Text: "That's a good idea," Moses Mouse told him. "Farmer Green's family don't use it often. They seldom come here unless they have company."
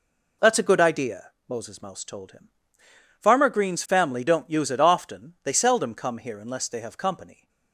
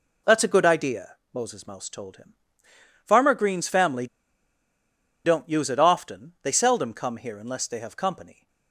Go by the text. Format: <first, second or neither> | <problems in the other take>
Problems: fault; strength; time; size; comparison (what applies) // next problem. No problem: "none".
first | pauses between "family" and "don't"; at 4.0 s; 1.1 s long